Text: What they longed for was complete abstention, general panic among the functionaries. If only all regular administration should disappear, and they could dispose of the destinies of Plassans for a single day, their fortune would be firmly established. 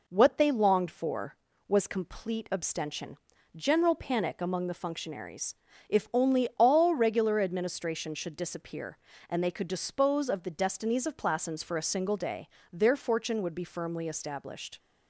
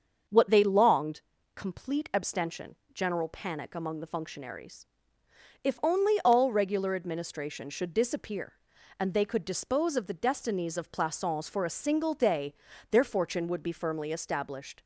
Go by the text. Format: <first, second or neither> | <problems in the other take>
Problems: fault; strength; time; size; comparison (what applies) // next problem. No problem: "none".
first | starts louder than the rest; until 1.6 s; 6.5 dB // skips "for was"; at 1.3 s